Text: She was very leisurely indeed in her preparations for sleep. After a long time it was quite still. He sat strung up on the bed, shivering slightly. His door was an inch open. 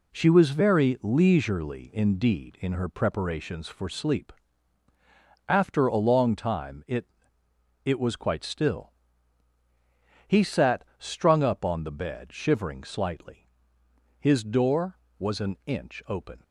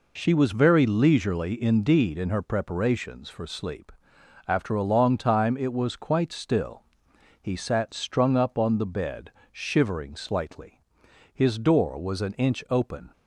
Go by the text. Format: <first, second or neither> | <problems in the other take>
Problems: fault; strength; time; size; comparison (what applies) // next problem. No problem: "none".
second | says "it" twice; at 7.8 s